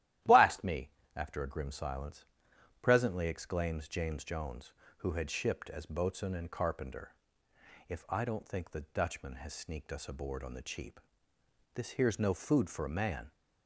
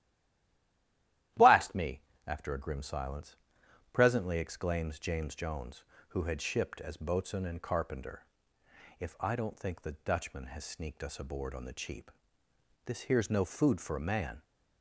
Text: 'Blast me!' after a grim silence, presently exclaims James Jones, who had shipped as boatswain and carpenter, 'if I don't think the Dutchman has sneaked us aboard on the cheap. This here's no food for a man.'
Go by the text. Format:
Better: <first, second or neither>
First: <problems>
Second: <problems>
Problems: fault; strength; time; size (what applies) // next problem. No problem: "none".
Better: first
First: starts louder than the rest; strong; until 1.4 s; 13.5 dB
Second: stays silent before the first word; noticeable; until 1.3 s; 1.3 s long // starts louder than the rest; strong; until 2.5 s; 13.5 dB